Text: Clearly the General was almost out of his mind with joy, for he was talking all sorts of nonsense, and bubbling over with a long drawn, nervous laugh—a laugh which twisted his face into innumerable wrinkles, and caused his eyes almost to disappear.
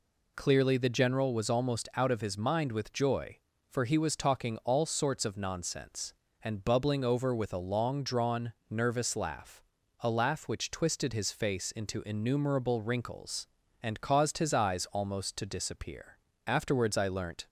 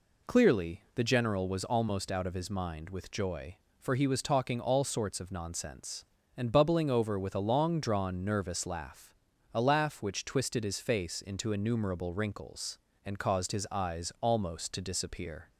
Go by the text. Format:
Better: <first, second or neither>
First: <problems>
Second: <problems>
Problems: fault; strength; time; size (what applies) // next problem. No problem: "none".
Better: second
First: goes on to say "Afterwards I learnt"; noticeable; from 16.4 s on; 1.0 s long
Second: none